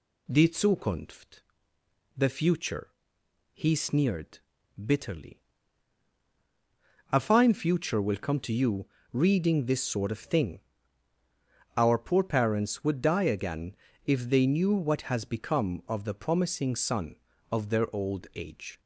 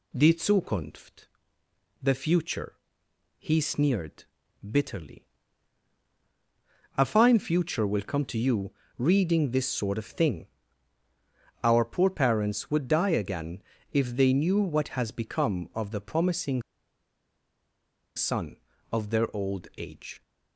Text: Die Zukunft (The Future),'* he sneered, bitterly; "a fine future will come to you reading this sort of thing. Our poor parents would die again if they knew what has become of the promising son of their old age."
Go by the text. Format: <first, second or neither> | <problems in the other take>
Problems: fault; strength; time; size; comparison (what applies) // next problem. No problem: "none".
first | pauses between "you" and "reading"; slight; at 8.7 s; 0.26 s long; slight in the first // pauses between "again" and "if"; slight; at 13.6 s; 0.32 s long; slight in the first // pauses between "promising" and "son"; strong; at 16.6 s; 1.5 s long